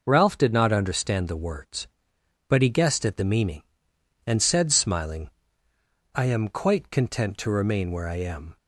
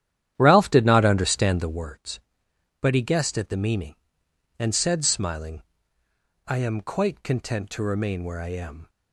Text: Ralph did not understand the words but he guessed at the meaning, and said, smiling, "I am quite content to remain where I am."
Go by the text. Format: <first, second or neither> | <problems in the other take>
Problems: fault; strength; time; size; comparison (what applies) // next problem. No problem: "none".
first | starts louder than the rest; strong; until 1.9 s; 11 dB